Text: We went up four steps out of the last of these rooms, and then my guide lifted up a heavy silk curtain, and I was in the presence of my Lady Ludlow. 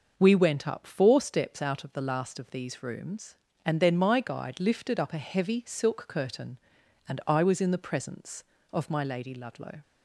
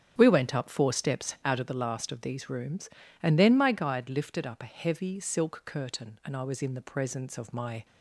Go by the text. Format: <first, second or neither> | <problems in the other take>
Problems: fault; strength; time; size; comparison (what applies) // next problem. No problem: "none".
first | starts louder than the rest; strong; until 1.1 s; 8 dB; also in the first // stops before "Lady Ludlow"; at 7.8 s